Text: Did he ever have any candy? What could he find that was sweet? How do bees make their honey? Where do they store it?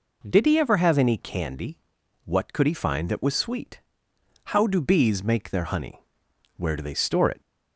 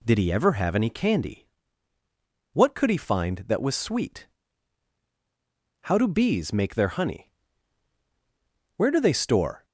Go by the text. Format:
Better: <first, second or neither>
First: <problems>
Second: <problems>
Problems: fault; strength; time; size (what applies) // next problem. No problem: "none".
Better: first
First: none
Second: stops before "it"; at 9.6 s